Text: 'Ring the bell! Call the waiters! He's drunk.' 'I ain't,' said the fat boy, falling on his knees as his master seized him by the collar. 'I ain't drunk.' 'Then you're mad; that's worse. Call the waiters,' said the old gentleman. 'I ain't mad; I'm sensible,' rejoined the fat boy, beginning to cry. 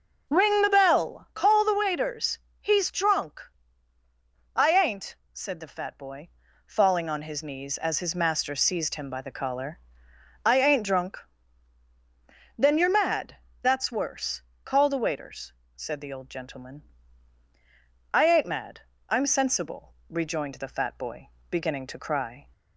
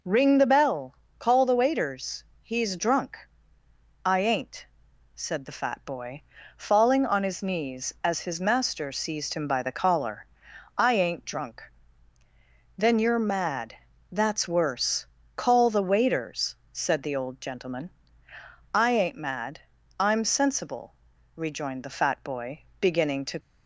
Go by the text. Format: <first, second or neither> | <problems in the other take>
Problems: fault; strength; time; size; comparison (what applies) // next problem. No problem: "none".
first | stops before "cry"; at 23.4 s